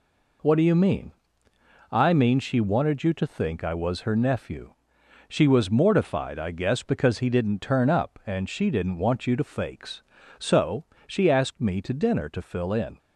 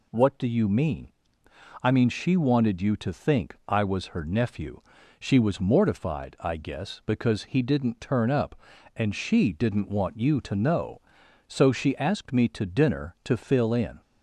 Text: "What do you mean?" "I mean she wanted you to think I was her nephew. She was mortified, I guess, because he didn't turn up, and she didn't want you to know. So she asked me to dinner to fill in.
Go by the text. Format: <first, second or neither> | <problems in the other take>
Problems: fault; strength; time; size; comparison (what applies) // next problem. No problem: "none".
second | says "fakes" for "know"; at 9.4 s // pauses between "So" and "she"; slight; at 10.8 s; 0.24 s long